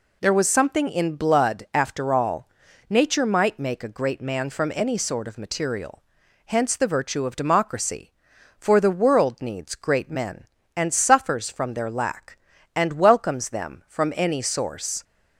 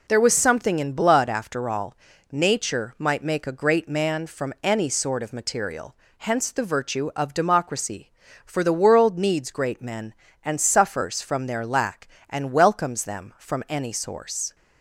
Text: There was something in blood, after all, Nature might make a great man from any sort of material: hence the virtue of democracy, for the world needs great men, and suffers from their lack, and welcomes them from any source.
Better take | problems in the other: neither | none

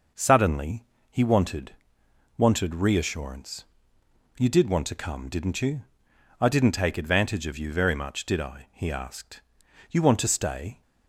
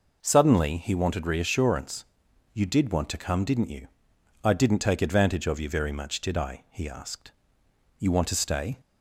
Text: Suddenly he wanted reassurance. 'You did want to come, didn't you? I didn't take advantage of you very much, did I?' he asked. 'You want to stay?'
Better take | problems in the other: second | pauses between "Suddenly" and "he"; slight; at 0.8 s; 0.24 s long // says "wanted" twice; at 2.3 s

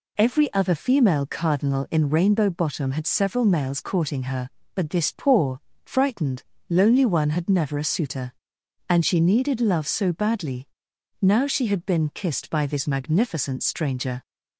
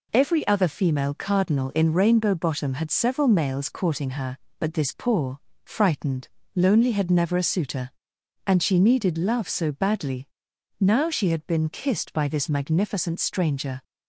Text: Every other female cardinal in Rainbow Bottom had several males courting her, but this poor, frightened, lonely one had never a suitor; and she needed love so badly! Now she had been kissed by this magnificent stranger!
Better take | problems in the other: first | skips "one"; at 6.9 s

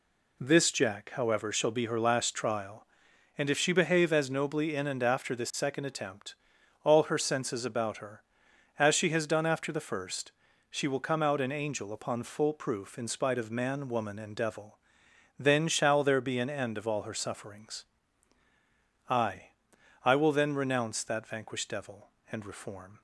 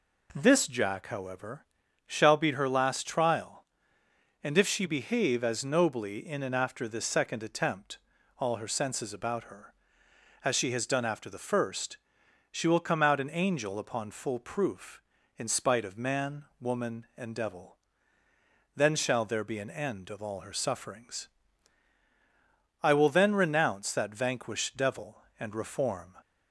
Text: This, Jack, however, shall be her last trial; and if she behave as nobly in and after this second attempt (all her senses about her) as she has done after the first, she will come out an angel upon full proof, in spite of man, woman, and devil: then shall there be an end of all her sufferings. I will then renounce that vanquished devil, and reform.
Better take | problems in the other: second | says "I" twice; at 20.0 s

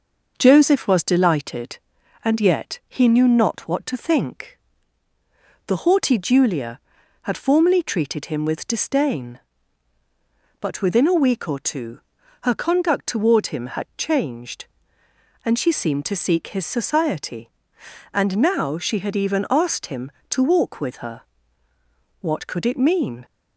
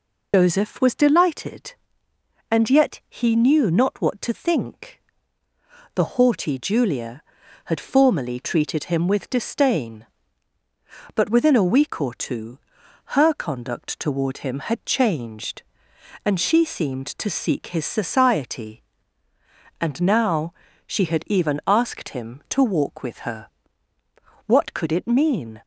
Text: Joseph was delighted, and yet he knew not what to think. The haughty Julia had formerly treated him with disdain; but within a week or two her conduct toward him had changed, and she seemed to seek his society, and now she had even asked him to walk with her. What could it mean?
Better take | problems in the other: first | loses the start of "Joseph"; at 0.3 s; 105 ms // pauses between "two" and "her"; noticeable; at 12.5 s; 0.56 s long; also in the first // pauses between "now" and "she"; slight; at 20.5 s; 0.32 s long

